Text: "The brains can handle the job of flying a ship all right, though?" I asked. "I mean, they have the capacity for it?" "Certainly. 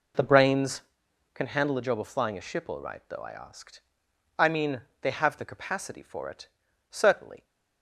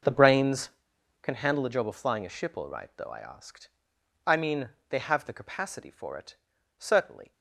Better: first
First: none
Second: gets quieter; strong; throughout; 14.5 dB

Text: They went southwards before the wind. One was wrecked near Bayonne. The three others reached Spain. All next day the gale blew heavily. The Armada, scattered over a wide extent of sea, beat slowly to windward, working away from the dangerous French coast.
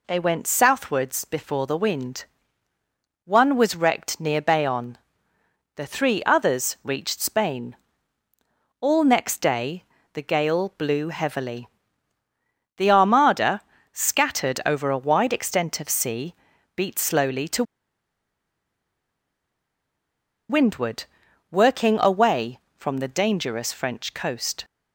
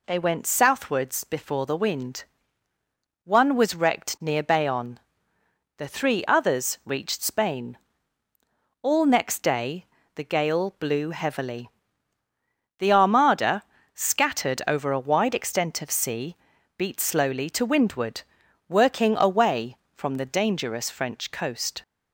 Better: second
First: pauses between "day" and "the"; slight; at 9.8 s; 0.30 s long // pauses between "to" and "windward"; strong; at 17.6 s; 2.8 s long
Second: pauses between "day" and "the"; slight; at 9.8 s; 0.30 s long

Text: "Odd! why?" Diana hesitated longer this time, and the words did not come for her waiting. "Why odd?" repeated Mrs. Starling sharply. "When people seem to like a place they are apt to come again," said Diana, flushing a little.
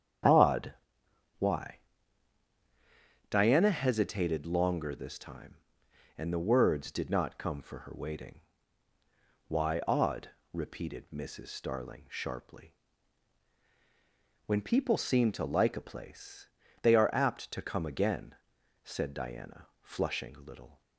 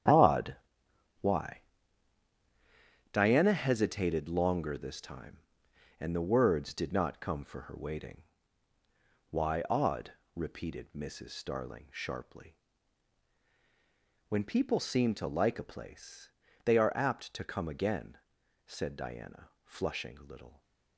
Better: first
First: starts louder than the rest; strong; until 3.3 s; 8.5 dB // pauses between "place" and "they"; slight; at 16.4 s; 0.32 s long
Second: gets quieter; strong; throughout; 11.5 dB // starts louder than the rest; strong; until 3.2 s; 9.5 dB // pauses between "place" and "they"; slight; at 16.3 s; 0.32 s long

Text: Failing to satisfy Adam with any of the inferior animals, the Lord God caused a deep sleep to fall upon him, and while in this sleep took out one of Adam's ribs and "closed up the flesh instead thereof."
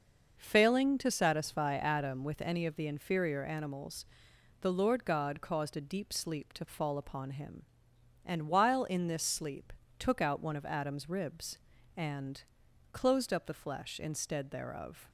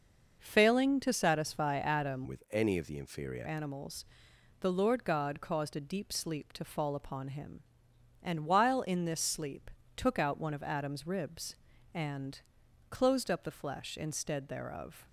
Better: first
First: pauses between "sleep" and "took"; slight; at 9.7 s; 0.24 s long // pauses between "and" and "closed"; noticeable; at 12.4 s; 0.50 s long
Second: starts louder than the rest; noticeable; until 1.4 s; 6 dB // changes voice from "with" to "inferior"; from 2.2 to 3.4 s; 1.2 s long // pauses between "sleep" and "took"; slight; at 9.7 s; 0.24 s long // pauses between "and" and "closed"; noticeable; at 12.4 s; 0.50 s long

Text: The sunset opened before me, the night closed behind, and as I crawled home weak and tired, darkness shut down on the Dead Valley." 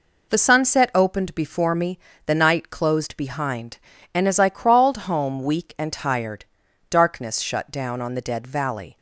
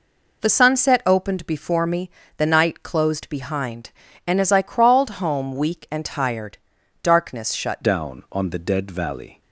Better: first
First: none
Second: changes voice at "down"; from 7.8 s on; 1.6 s long

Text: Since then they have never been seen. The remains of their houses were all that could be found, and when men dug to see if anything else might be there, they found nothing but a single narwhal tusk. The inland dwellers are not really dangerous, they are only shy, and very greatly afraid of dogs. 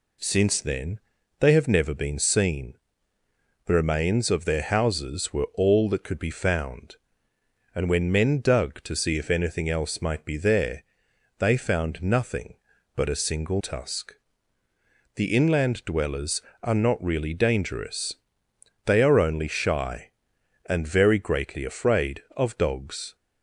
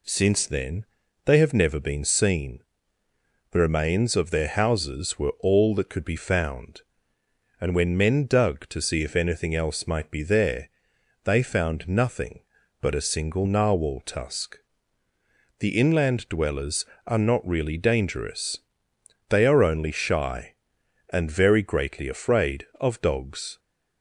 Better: second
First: pauses between "then" and "they"; at 0.9 s; 0.40 s long // skips "narwhal"; at 13.6 s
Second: pauses between "then" and "they"; at 0.8 s; 0.40 s long

